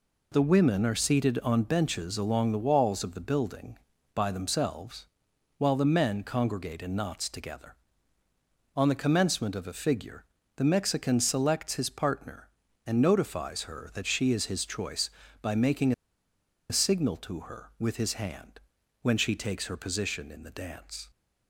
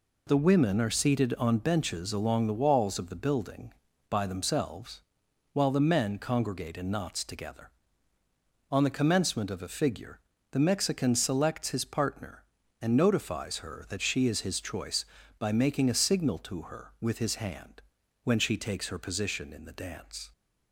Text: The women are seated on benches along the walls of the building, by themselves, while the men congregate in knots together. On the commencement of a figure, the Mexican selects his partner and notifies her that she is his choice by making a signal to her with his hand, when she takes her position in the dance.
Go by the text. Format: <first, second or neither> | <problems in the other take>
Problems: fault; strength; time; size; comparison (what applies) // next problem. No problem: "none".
second | pauses between "making" and "a"; noticeable; at 15.9 s; 0.77 s long